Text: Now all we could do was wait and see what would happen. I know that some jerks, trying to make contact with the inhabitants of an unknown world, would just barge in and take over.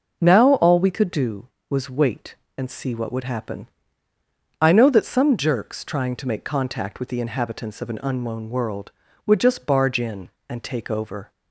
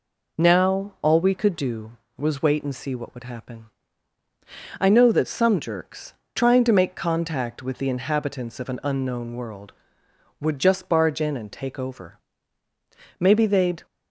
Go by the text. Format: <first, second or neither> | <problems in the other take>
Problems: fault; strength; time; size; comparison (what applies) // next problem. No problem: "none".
first | goes on to say "Maybe they'd"; noticeable; from 13.1 s on; 0.66 s long